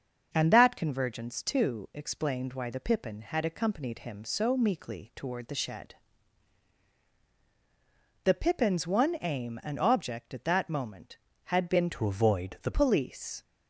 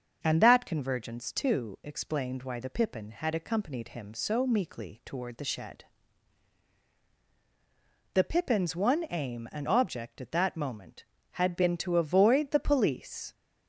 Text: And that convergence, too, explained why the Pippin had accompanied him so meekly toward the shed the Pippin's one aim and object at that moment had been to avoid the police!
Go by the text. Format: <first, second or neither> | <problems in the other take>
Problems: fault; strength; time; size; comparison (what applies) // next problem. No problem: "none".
second | starts louder than the rest; until 1.3 s; 6.5 dB; also in the second // pauses between "shed" and "the"; strong; at 5.9 s; 2.2 s long; strong in the second // changes voice from "to" to "the"; from 11.9 to 12.7 s; 0.8 s long